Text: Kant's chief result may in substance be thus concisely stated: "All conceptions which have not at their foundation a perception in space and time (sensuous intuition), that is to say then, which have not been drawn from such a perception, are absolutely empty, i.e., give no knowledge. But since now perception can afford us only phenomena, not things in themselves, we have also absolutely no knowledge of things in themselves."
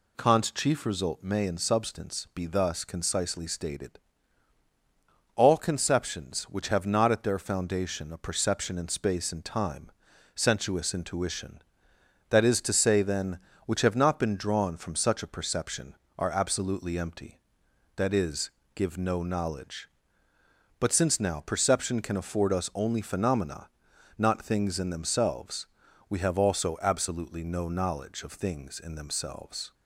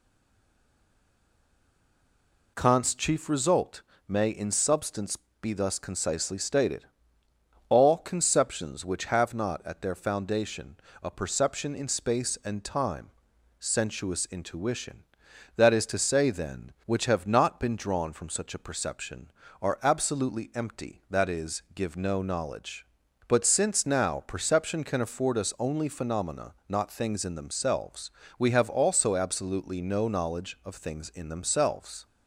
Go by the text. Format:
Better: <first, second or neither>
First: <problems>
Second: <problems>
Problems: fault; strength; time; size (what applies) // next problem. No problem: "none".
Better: first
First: none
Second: stays silent before the first word; strong; until 2.5 s; 2.5 s long // pauses between "result" and "may"; slight; at 3.8 s; 0.26 s long // pauses between "substance" and "be"; slight; at 5.1 s; 0.24 s long // pauses between "foundation" and "a"; slight; at 10.7 s; 0.26 s long